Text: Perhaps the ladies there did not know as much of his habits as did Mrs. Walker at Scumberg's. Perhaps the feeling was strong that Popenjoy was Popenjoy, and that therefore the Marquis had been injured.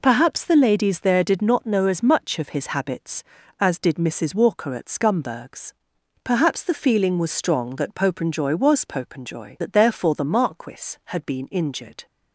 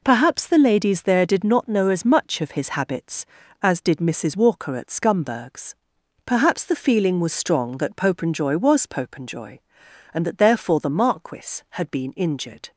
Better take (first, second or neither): second